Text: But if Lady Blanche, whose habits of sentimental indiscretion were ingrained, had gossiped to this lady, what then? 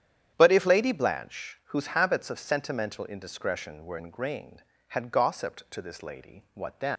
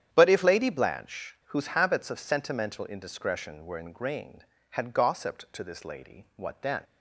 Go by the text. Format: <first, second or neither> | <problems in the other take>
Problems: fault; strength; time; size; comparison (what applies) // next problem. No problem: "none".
second | starts louder than the rest; strong; until 1.3 s; 9.5 dB; strong in the second // leaves "then" unfinished; at 6.9 s; 60 ms